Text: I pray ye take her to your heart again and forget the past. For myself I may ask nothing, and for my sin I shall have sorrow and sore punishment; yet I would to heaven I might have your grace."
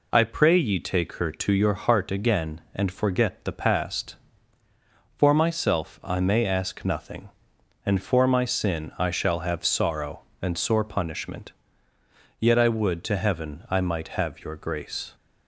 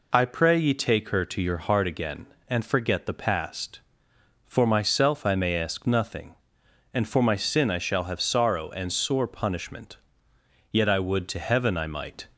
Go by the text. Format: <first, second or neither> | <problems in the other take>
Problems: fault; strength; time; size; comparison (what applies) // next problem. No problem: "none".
first | stops before "have your grace"; at 12.3 s